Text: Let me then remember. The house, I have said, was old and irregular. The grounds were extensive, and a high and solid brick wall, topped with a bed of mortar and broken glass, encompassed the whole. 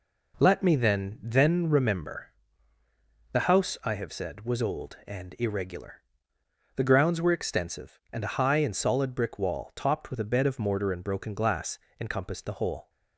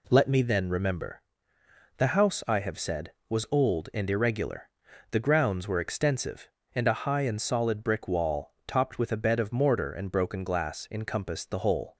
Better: second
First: says "then" twice; at 1.2 s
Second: none

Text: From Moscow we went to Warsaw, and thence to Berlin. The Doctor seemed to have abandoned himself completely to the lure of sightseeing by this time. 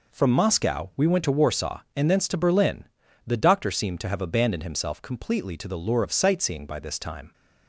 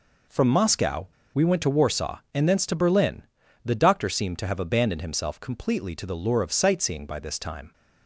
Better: first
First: none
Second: pauses between "Moscow" and "we"; slight; at 1.0 s; 0.28 s long

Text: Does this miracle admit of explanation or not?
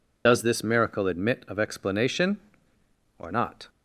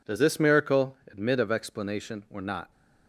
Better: second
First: loses the start of "Does"; at 0.2 s; 30 ms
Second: none

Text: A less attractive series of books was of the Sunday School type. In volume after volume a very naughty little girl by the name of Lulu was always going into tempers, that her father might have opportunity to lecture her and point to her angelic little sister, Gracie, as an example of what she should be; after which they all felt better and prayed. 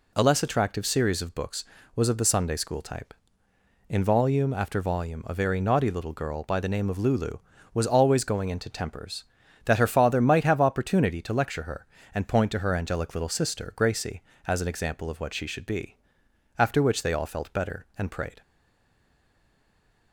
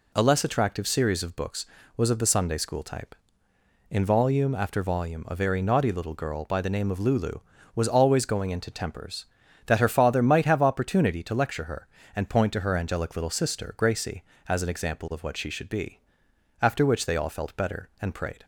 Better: second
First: stays silent after the last word; noticeable; from 18.4 s on; 1.7 s long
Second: none

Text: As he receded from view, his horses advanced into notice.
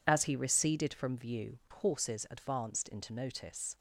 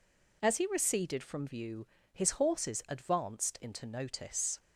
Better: second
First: skips "his"; at 1.6 s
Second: none

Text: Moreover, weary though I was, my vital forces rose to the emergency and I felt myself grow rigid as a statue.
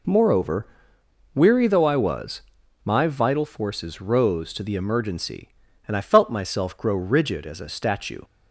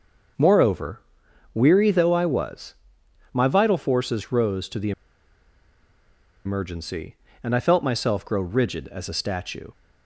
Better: first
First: none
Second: starts louder than the rest; until 1.8 s; 6.5 dB // pauses between "the" and "emergency"; strong; at 4.9 s; 1.5 s long

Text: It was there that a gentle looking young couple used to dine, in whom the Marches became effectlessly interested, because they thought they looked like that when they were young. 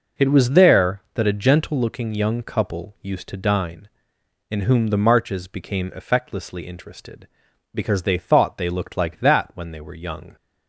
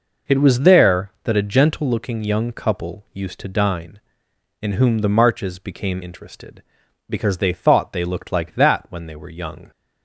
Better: first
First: none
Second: skips "effectlessly"; at 6.0 s

